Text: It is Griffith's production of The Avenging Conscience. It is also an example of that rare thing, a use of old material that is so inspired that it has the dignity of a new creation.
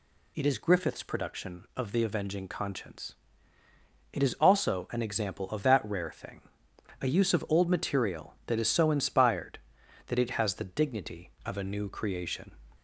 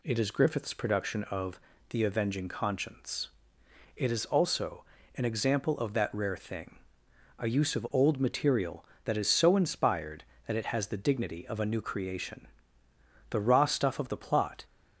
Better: first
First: none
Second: pauses between "of" and "The"; slight; at 1.5 s; 0.32 s long // pauses between "also" and "an"; slight; at 4.8 s; 0.32 s long // goes on to say "The raw stuff of the plot"; from 13.3 s on; 1.3 s long

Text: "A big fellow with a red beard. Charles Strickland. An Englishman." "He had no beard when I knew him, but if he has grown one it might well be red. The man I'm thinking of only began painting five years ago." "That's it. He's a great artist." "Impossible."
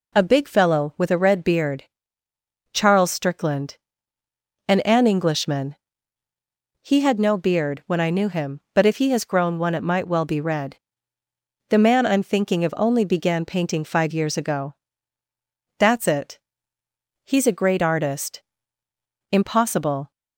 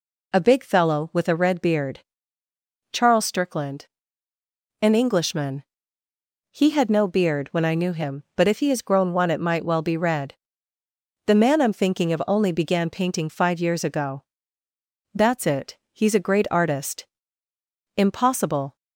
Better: second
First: says "An" twice; at 4.8 s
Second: none

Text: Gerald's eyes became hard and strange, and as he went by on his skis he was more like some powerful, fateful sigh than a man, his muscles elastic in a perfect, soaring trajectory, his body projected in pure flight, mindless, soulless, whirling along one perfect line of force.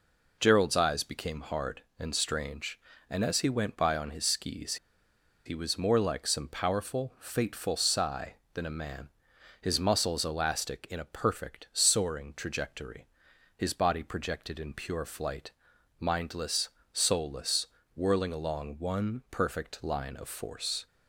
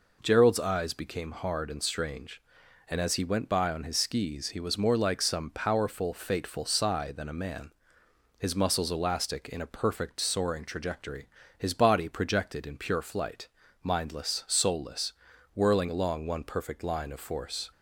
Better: second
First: pauses between "skis" and "he"; noticeable; at 4.7 s; 0.69 s long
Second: none

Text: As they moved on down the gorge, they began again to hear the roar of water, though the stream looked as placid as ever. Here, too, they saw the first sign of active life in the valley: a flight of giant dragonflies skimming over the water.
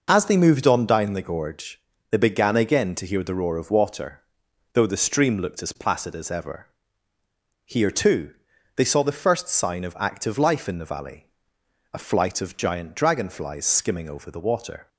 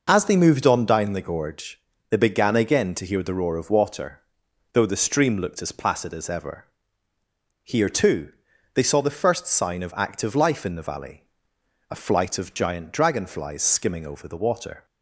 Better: neither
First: none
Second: none

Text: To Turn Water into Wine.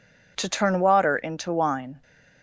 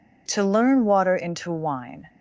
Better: first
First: none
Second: says "Learn" for "Turn"; at 0.4 s

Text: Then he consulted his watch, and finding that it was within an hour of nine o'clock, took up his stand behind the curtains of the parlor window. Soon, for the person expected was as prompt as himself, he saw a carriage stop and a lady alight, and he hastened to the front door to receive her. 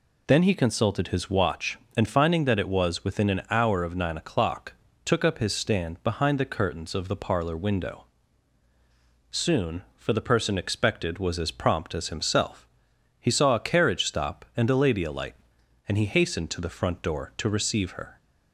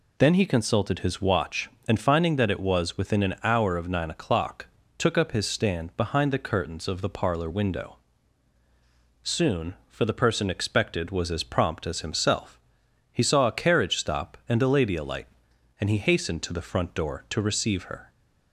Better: neither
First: none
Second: none

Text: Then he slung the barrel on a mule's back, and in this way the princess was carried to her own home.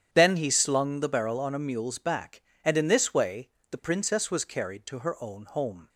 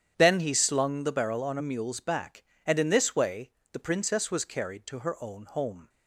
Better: neither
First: starts louder than the rest; strong; until 1.1 s; 9 dB // pauses between "way" and "the"; slight; at 3.4 s; 0.22 s long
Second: starts louder than the rest; strong; until 1.1 s; 9 dB // pauses between "way" and "the"; slight; at 3.5 s; 0.22 s long

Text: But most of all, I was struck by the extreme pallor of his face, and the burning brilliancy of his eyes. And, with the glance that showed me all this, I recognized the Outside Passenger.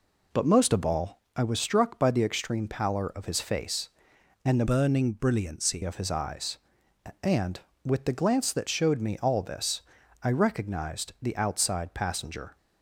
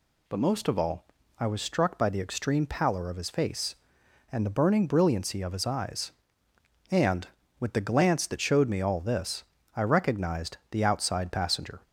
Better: second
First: changes voice from "burning" to "brilliancy"; from 4.6 to 5.8 s; 1.2 s long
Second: none

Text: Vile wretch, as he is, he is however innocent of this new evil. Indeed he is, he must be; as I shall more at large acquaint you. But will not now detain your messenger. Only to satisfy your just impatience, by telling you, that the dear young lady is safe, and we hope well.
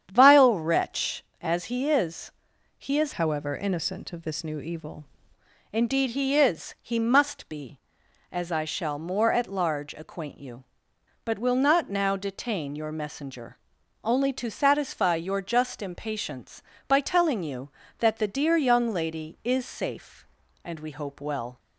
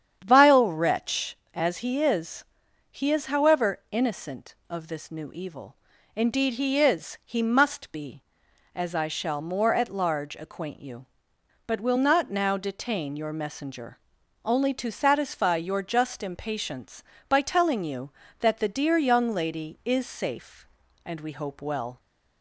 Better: second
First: starts louder than the rest; strong; until 1.1 s; 8.5 dB // changes voice from "however" to "evil"; from 3.1 to 5.0 s; 1.9 s long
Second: starts louder than the rest; strong; until 1.2 s; 8.5 dB

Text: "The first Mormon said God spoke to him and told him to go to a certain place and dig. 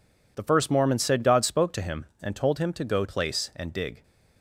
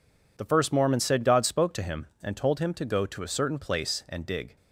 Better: second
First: skips "to a certain"; at 3.0 s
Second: none

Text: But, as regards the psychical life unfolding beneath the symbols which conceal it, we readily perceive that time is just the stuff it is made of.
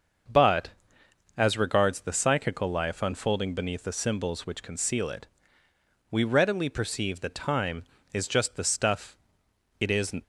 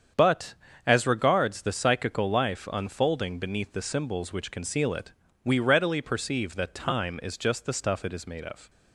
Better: second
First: starts louder than the rest; until 1.9 s; 6.5 dB // pauses between "stuff" and "it"; noticeable; at 9.1 s; 0.62 s long // stops before "made of"; at 10.2 s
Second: starts louder than the rest; strong; until 1.4 s; 7.5 dB

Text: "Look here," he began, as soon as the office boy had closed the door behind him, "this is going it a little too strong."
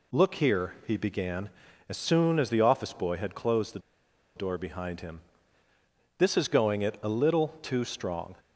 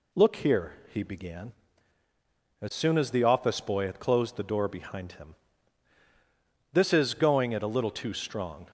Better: second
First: pauses between "the" and "door"; noticeable; at 3.7 s; 0.57 s long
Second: none

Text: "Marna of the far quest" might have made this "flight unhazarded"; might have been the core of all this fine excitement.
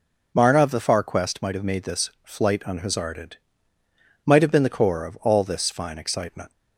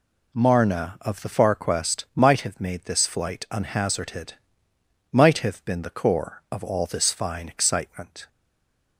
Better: first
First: none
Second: stays silent after the last word; slight; from 8.2 s on; 0.7 s long

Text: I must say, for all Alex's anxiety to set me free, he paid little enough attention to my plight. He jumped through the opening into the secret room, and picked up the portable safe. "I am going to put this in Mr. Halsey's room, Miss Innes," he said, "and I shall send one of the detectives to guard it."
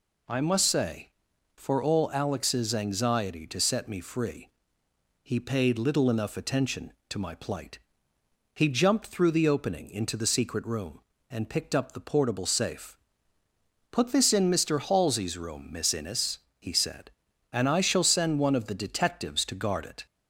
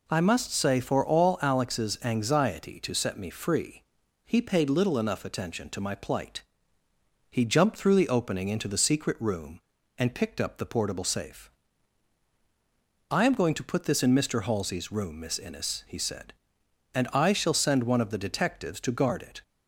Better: second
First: skips "I am going to"; at 13.4 s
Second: none

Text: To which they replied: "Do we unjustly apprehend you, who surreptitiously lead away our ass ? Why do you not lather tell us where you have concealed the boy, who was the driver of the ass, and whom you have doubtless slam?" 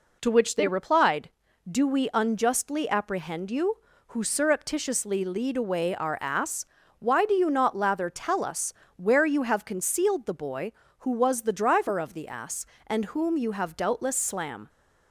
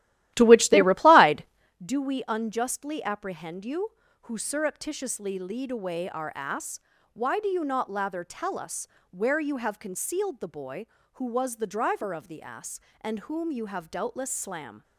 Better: first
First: pauses between "us" and "where"; slight; at 8.7 s; 0.24 s long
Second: starts louder than the rest; strong; until 1.8 s; 14.5 dB // pauses between "us" and "where"; slight; at 8.8 s; 0.24 s long

